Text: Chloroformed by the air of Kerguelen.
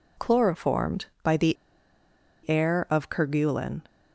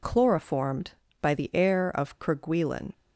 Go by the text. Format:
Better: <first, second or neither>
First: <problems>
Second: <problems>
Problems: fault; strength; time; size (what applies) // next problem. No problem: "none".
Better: second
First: pauses between "the" and "air"; noticeable; at 1.5 s; 0.93 s long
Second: none